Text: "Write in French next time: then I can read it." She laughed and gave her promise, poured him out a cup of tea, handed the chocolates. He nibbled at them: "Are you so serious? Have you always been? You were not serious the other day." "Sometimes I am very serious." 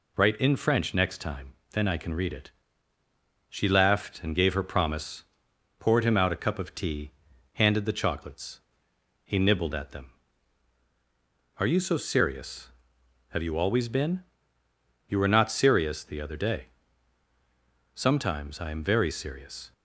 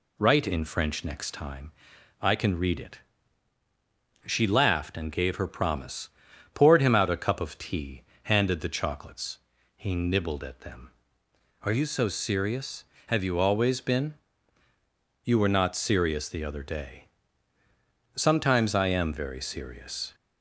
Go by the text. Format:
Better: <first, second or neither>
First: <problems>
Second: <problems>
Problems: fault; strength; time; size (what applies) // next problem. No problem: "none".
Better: first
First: none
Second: skips "then"; at 1.9 s